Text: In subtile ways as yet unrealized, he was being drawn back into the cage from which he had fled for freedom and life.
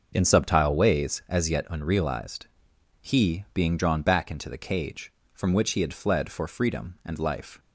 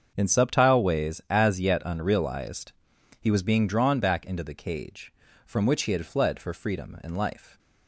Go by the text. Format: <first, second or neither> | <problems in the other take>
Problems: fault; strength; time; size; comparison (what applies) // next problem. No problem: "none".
second | starts louder than the rest; until 1.1 s; 6.5 dB; also in the second // skips "was"; at 3.5 s